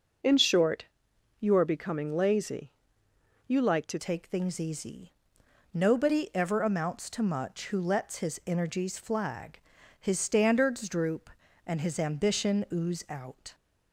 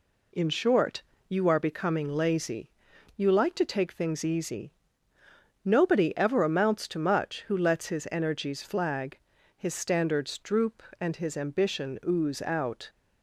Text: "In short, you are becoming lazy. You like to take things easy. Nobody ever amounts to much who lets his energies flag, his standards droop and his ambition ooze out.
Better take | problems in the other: second | changes voice at "take"; from 3.9 s on; 9.6 s long

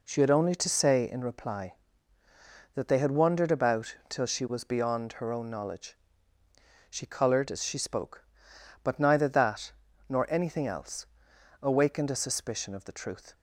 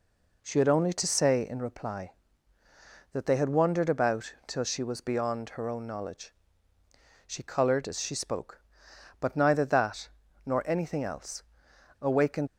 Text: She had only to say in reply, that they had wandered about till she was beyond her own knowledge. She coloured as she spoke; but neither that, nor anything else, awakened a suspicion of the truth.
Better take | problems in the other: first | stops before "a suspicion of the truth"; at 12.4 s

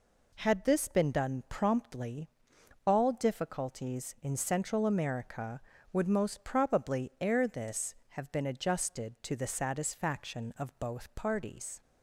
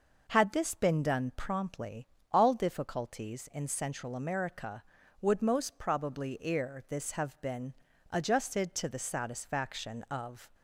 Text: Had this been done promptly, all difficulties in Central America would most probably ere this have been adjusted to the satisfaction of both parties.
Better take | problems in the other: first | pauses between "been" and "adjusted"; at 7.7 s; 0.38 s long // stops before "both parties"; at 10.5 s

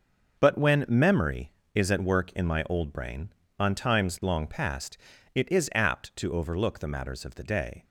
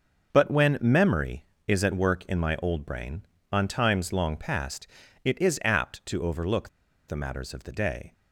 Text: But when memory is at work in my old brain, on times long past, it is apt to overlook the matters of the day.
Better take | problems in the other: first | starts louder than the rest; until 1.3 s; 6.5 dB; also in the first // pauses between "overlook" and "the"; at 6.6 s; 0.39 s long

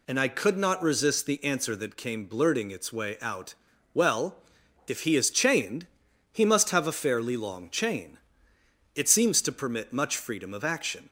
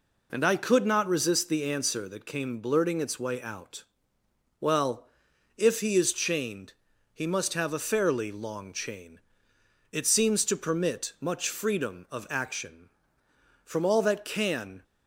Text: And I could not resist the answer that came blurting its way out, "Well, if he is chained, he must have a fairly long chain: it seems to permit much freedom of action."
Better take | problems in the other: first | goes on to say "From all that can"; noticeable; from 13.6 s on; 1.1 s long

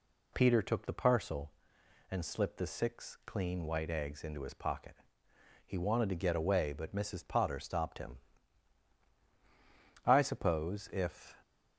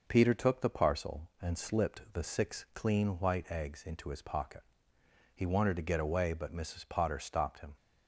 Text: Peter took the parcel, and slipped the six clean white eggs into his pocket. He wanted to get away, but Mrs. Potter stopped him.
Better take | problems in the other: second | goes on to say "I suppose if"; from 10.0 s on; 1.3 s long

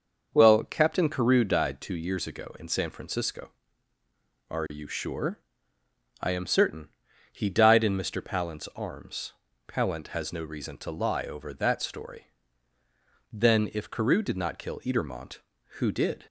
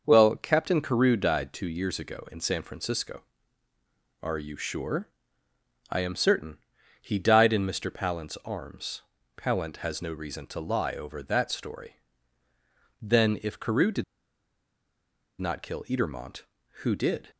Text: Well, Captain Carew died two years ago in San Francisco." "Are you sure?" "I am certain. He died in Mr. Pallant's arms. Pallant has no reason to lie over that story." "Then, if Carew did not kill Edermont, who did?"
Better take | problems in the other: first | pauses between "did" and "not"; strong; at 14.0 s; 1.3 s long

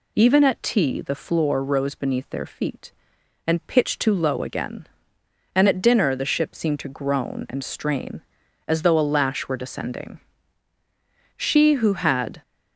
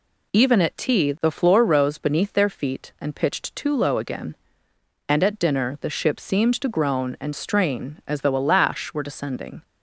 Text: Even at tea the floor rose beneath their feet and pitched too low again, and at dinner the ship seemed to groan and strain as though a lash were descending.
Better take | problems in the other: second | goes on to say "She who had"; noticeable; from 11.3 s on; 1.0 s long

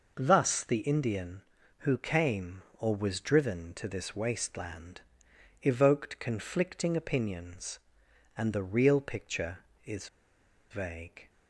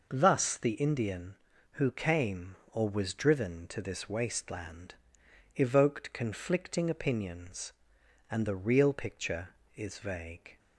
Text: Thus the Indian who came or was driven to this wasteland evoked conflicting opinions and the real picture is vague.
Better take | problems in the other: second | pauses between "wasteland" and "evoked"; noticeable; at 4.9 s; 0.62 s long; noticeable in the second // pauses between "is" and "vague"; noticeable; at 10.0 s; 0.62 s long

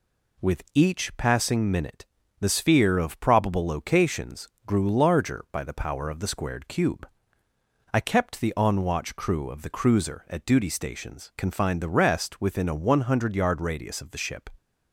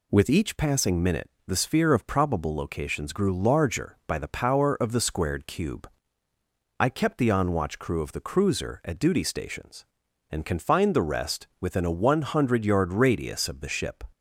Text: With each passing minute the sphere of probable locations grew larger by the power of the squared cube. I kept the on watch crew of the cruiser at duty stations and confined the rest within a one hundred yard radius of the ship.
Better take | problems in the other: second | pauses between "minute" and "the"; slight; at 2.0 s; 0.34 s long; slight in the second // pauses between "locations" and "grew"; slight; at 4.4 s; 0.20 s long // skips "and"; at 11.3 s

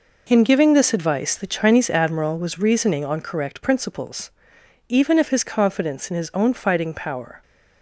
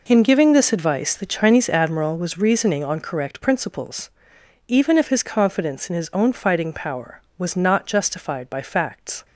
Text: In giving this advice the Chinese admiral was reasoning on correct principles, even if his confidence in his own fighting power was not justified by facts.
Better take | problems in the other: second | stops before "was not justified by facts"; at 7.4 s

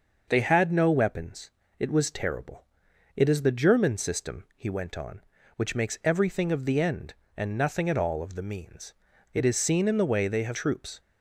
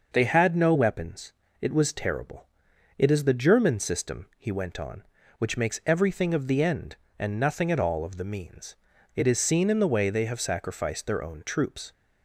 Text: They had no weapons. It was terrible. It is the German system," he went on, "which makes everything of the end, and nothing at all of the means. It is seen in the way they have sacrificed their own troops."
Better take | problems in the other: second | skips "sacrificed their own"; at 10.5 s

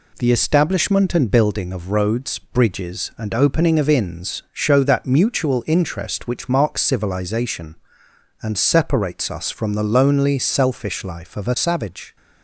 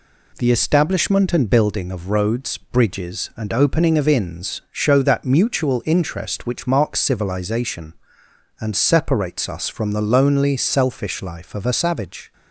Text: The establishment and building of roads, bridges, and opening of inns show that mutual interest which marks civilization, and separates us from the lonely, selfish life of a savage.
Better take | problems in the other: neither | none

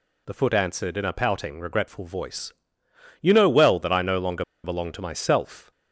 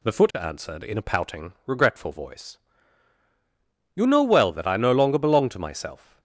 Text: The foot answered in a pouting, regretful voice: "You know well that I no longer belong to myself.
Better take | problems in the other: second | pauses between "longer" and "belong"; slight; at 4.4 s; 0.20 s long

